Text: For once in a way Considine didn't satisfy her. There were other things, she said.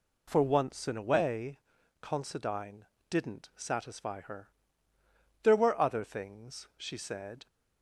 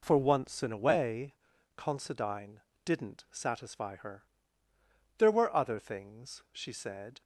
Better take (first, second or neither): first